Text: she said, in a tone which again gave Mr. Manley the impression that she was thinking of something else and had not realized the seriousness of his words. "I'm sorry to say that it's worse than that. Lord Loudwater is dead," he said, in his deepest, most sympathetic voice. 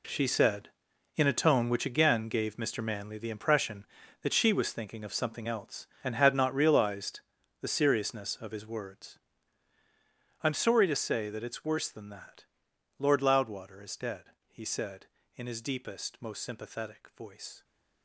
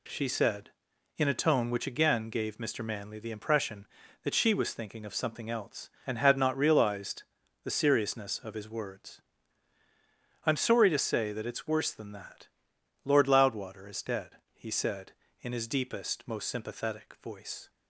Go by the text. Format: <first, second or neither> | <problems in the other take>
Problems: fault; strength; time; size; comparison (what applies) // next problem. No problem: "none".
second | gets quieter; strong; throughout; 12 dB // pauses between "realized" and "the"; at 7.1 s; 0.42 s long; also in the second